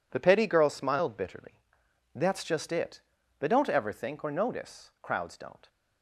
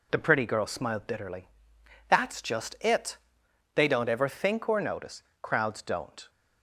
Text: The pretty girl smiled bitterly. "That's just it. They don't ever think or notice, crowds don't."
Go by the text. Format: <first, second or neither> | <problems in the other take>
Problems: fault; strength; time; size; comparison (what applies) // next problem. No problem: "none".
second | says "petty" for "pretty"; at 0.1 s